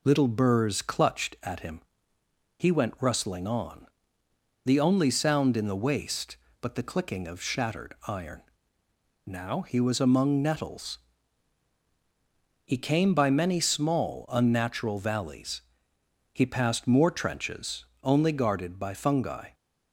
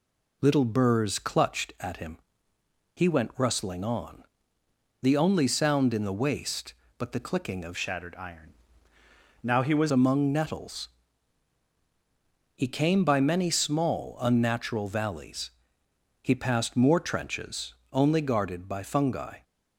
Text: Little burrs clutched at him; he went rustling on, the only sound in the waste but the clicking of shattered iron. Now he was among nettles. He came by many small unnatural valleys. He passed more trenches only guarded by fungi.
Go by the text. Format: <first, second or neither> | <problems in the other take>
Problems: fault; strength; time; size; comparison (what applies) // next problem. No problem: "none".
first | changes voice from "shattered" to "was"; from 7.7 to 9.9 s; 2.2 s long // pauses between "trenches" and "only"; slight; at 17.7 s; 0.16 s long; slight in the first